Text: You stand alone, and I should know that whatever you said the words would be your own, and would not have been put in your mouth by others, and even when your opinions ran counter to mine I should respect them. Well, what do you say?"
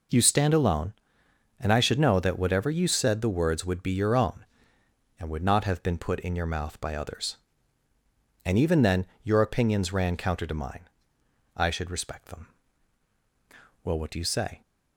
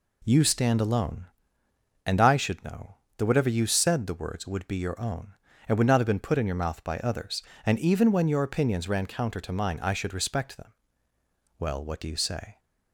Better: second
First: says "then" for "when"; at 8.8 s // pauses between "mine" and "I"; noticeable; at 10.8 s; 0.70 s long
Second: none

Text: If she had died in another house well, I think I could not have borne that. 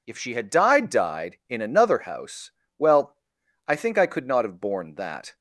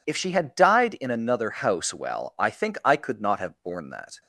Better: second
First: says "died" twice; at 0.8 s // pauses between "house" and "well"; slight; at 2.5 s; 0.26 s long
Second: none

